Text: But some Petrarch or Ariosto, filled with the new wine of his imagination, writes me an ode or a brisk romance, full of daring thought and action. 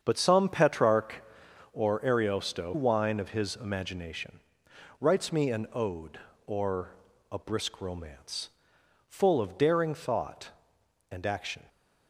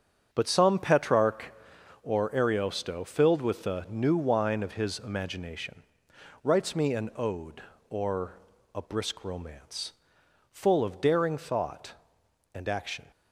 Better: second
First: starts louder than the rest; strong; until 1.0 s; 7.5 dB // skips "filled with the new"; at 2.7 s // pauses between "or" and "a"; slight; at 6.9 s; 0.36 s long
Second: starts louder than the rest; strong; until 1.3 s; 7.5 dB // pauses between "or" and "a"; slight; at 8.3 s; 0.36 s long

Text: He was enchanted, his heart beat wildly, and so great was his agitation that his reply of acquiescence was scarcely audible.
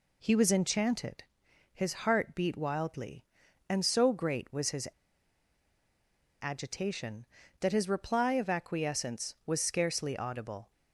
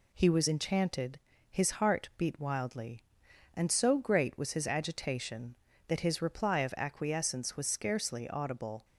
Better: second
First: pauses between "his" and "agitation"; strong; at 4.8 s; 1.5 s long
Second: none

